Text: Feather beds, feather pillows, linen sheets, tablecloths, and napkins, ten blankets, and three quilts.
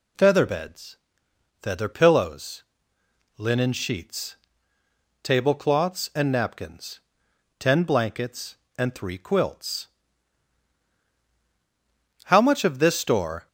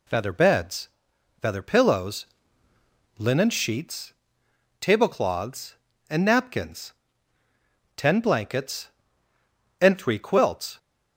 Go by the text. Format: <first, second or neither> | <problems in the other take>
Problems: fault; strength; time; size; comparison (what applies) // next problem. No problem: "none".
second | goes on to say "How much of this store"; noticeable; from 12.2 s on; 1.2 s long